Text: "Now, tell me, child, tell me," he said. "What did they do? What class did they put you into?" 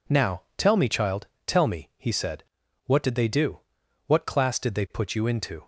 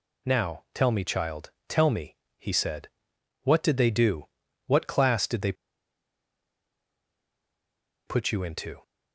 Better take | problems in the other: first | pauses between "they" and "put"; strong; at 5.5 s; 2.5 s long

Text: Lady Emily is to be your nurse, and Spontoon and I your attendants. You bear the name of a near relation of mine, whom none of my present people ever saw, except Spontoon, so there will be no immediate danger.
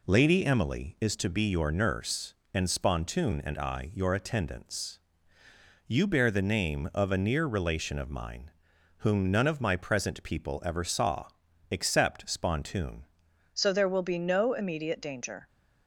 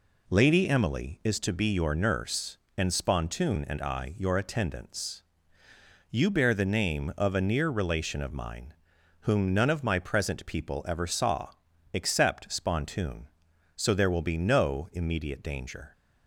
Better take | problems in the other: second | changes voice at "so"; from 13.5 s on; 1.9 s long

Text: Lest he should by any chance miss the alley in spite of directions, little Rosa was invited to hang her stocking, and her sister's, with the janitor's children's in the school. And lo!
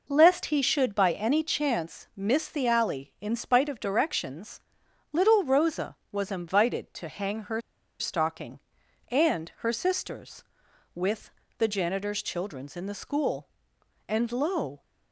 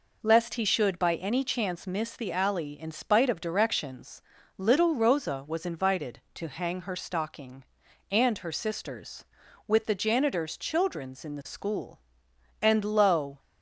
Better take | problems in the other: second | pauses between "her" and "stocking"; at 7.6 s; 0.38 s long // pauses between "with" and "the"; slight; at 11.3 s; 0.26 s long

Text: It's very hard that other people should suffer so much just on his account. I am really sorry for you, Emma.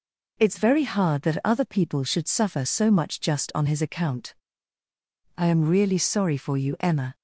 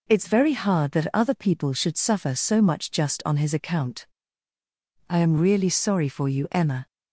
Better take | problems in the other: neither | none

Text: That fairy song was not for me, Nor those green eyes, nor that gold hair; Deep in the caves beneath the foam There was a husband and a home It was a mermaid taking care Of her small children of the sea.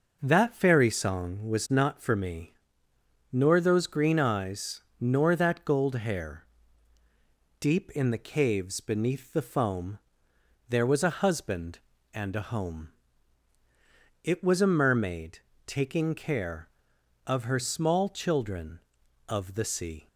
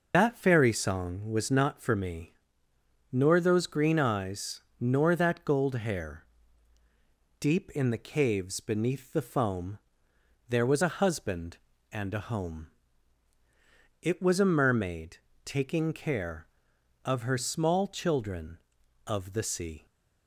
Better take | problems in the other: first | loses the start of "That"; at 0.1 s; 115 ms // pauses between "foam" and "There"; noticeable; at 9.7 s; 0.72 s long; noticeable in the first // pauses between "home" and "It"; strong; at 12.6 s; 1.3 s long; strong in the first // pauses between "mermaid" and "taking"; slight; at 15.1 s; 0.26 s long; slight in the first

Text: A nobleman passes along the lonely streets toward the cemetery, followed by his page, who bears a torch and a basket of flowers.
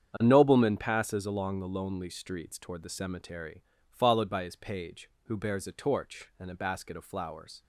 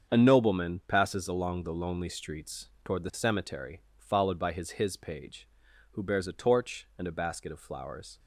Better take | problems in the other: first | starts louder than the rest; strong; until 1.1 s; 7.5 dB; strong in the first // pauses between "streets" and "toward"; slight; at 2.6 s; 0.16 s long // says "his" twice; at 4.7 s

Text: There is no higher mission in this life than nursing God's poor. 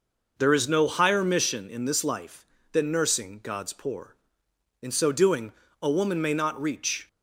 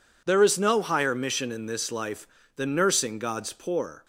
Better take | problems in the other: second | goes on to say "In so doing a woman may not reach"; strong; from 4.8 s on; 2.2 s long

